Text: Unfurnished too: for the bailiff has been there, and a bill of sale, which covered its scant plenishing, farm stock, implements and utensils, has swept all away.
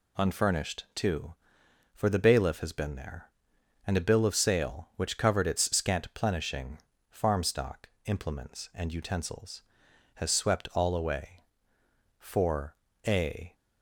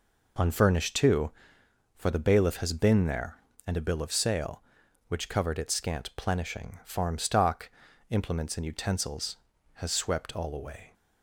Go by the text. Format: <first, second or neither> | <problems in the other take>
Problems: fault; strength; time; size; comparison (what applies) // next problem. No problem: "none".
second | goes on to say "For a"; from 12.1 s on; 1.3 s long